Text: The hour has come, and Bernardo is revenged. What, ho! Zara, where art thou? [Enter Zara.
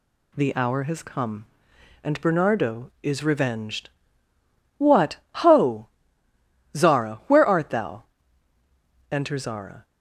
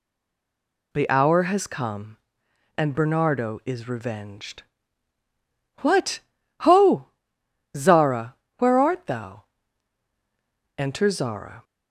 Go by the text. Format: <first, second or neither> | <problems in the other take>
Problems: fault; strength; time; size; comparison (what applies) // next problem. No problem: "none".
first | stays silent before the first word; slight; until 0.9 s; 0.9 s long